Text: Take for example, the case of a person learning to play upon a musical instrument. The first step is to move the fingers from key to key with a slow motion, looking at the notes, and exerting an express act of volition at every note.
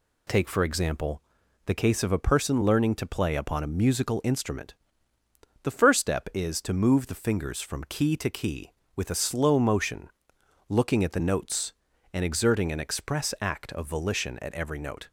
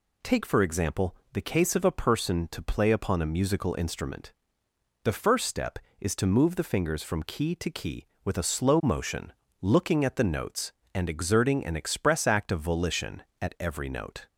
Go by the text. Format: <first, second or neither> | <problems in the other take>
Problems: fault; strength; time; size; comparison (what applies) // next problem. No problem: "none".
first | skips "learning"; at 2.4 s